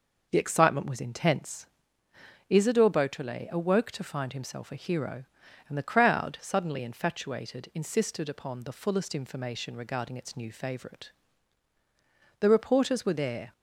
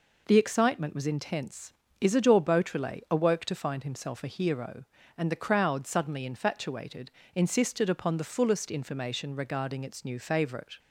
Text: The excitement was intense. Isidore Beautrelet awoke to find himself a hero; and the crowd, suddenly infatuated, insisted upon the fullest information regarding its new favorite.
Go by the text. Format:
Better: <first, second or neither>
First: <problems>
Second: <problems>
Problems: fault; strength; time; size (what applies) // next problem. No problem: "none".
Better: second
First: goes on to say "The reporters were there"; noticeable; from 12.3 s on; 1.1 s long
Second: none